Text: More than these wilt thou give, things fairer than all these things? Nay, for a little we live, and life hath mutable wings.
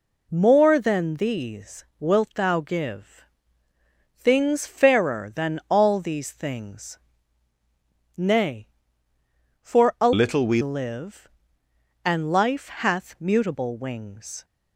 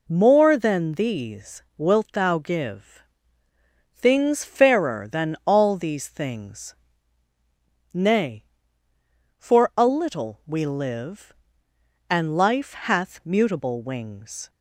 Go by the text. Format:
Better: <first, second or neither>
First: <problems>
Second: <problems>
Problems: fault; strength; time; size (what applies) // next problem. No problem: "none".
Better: second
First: changes voice from "little" to "we"; from 10.1 to 10.6 s; 0.5 s long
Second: none